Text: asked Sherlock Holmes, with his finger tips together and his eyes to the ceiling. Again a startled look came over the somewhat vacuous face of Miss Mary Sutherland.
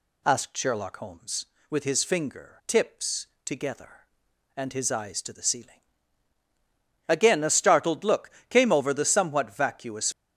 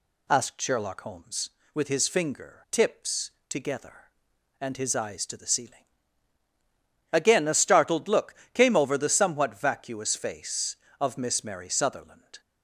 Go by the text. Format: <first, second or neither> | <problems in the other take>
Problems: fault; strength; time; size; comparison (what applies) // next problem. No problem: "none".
second | pauses between "tips" and "together"; slight; at 3.2 s; 0.18 s long; slight in the second // pauses between "look" and "came"; slight; at 8.3 s; 0.18 s long; slight in the second // stops before "face of Miss Mary Sutherland"; at 10.1 s